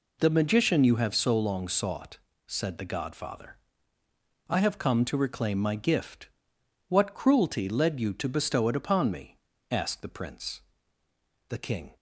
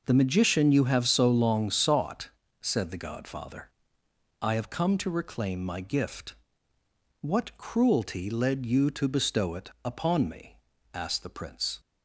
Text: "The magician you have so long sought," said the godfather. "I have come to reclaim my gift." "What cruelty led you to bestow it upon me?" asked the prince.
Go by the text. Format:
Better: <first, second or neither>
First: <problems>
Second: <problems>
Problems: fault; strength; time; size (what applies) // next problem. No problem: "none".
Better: second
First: goes on to say "The king"; slight; from 11.4 s on; 0.46 s long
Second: none